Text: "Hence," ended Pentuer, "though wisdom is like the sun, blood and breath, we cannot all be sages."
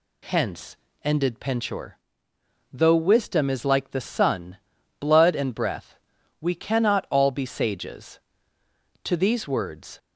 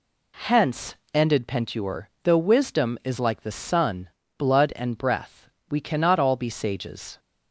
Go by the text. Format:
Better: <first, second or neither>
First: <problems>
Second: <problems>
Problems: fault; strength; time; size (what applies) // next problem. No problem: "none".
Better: second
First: goes on to say "To these words"; noticeable; from 9.0 s on; 0.96 s long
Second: none